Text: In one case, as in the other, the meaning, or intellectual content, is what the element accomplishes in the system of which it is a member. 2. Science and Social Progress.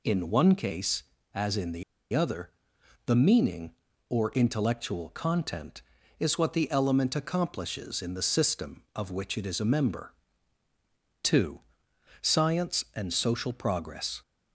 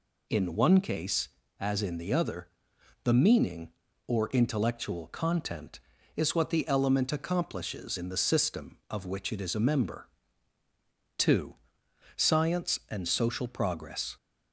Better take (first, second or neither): second